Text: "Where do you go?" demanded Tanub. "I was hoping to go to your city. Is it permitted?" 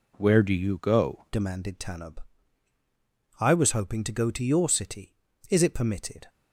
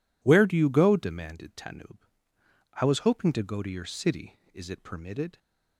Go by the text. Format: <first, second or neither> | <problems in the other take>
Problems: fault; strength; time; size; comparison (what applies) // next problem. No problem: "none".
second | changes voice at "demanded"; from 1.3 s on; 4.9 s long